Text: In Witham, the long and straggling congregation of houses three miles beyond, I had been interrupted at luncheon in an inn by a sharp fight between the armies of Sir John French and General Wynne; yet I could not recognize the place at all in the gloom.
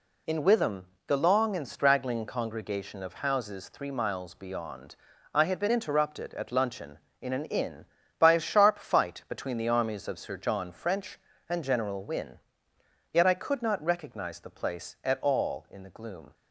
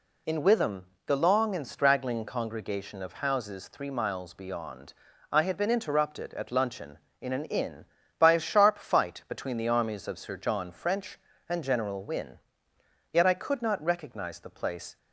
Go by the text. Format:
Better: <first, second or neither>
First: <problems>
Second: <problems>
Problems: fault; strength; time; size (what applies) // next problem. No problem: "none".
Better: first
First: none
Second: stops before "at all in the gloom"; at 14.9 s